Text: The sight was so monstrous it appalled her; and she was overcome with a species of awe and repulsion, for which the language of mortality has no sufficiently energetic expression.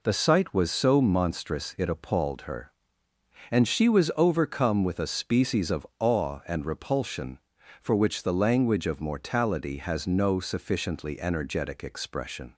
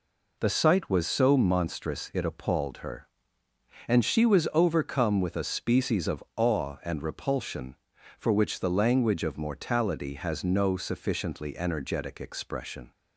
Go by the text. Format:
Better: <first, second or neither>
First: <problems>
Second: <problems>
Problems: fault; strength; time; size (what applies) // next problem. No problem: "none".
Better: neither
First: none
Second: none